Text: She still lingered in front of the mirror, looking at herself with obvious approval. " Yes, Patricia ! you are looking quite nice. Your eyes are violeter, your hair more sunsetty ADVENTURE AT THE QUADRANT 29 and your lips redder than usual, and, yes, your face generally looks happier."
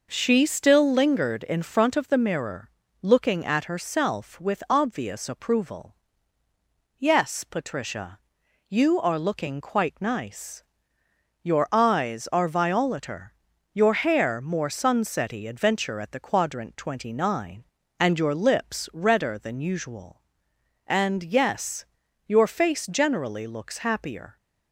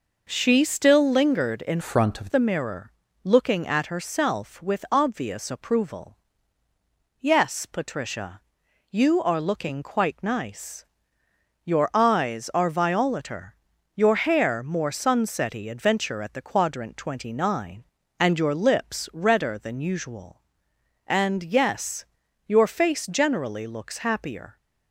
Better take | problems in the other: first | changes voice from "front" to "of"; from 1.8 to 2.3 s; 0.5 s long

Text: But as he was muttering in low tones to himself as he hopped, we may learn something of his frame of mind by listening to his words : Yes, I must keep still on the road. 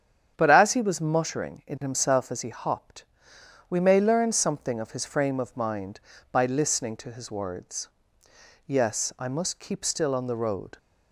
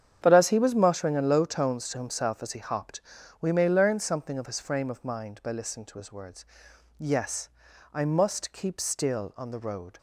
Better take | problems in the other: second | starts louder than the rest; strong; until 1.3 s; 8.5 dB; strong in the second // skips "low tones to"; at 1.7 s

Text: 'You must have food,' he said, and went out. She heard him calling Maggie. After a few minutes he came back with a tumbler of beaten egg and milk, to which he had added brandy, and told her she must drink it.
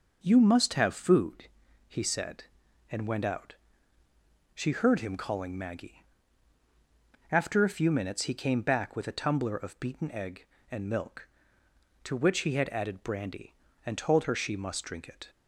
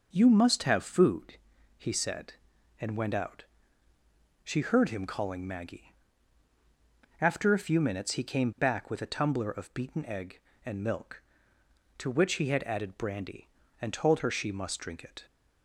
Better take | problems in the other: neither | none

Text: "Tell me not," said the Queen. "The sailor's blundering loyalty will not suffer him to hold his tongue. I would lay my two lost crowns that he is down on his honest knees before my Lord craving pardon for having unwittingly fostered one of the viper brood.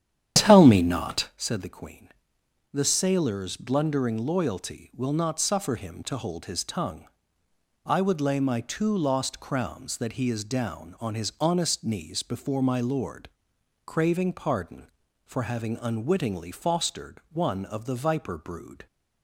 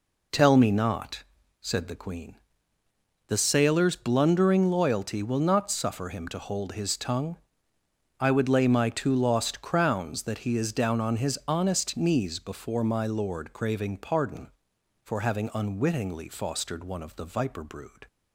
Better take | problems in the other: second | starts louder than the rest; strong; until 1.4 s; 10 dB // pauses between "Lord" and "craving"; noticeable; at 13.2 s; 0.58 s long

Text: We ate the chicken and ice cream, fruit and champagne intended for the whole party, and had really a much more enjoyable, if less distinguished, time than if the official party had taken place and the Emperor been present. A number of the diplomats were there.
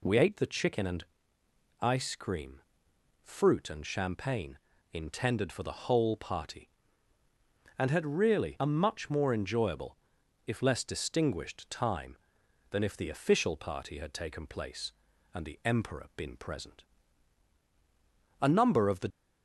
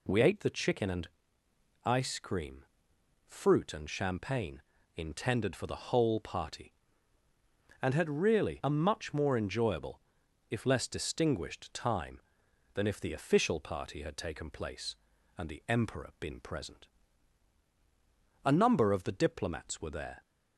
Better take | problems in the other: second | pauses between "and" and "ice"; noticeable; at 1.0 s; 0.74 s long; noticeable in the second // pauses between "champagne" and "intended"; slight; at 4.5 s; 0.34 s long; slight in the second // stops before "diplomats were there"; at 19.1 s

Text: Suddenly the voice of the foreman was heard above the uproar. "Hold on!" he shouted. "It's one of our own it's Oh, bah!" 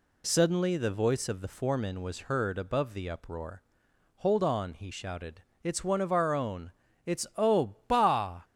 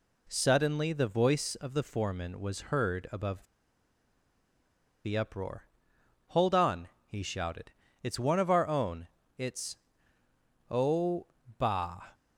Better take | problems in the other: first | pauses between "above" and "the"; strong; at 3.4 s; 1.6 s long // pauses between "own" and "it's"; slight; at 9.0 s; 0.30 s long; slight in the first // pauses between "it's" and "Oh"; noticeable; at 9.7 s; 0.92 s long

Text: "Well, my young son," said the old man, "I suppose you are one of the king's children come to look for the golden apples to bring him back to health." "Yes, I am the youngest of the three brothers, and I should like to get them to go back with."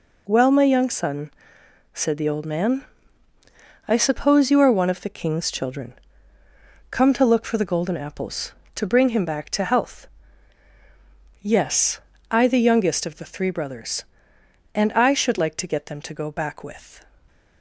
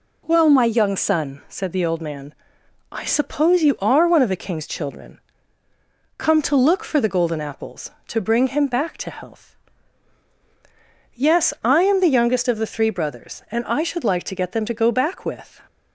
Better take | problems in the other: second | pauses between "children" and "come"; noticeable; at 5.9 s; 0.96 s long; noticeable in the second // skips "am"; at 12.4 s

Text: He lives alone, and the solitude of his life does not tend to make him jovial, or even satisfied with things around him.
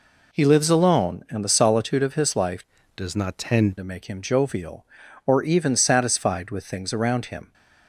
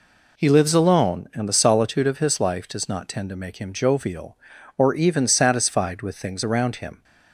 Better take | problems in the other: second | changes voice from "does" to "tend"; from 2.9 to 3.7 s; 0.8 s long

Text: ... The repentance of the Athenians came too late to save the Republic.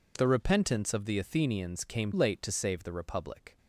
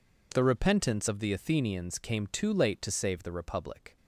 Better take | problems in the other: second | skips "too"; at 2.1 s

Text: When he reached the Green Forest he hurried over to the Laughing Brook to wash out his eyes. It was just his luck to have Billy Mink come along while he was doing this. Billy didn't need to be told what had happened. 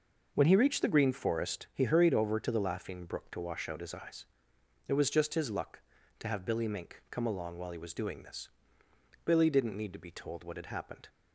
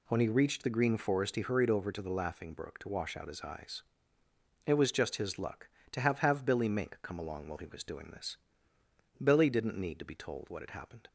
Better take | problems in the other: first | says "have" twice; at 6.1 s

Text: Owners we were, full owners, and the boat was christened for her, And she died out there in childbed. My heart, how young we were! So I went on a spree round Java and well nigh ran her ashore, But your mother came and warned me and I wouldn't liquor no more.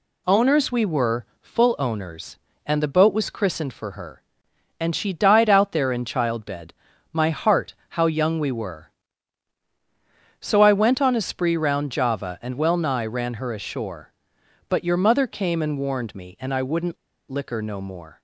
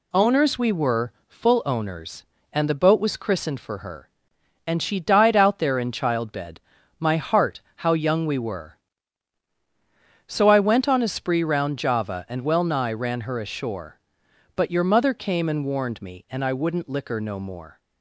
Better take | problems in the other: second | pauses between "wouldn't" and "liquor"; slight; at 16.9 s; 0.33 s long

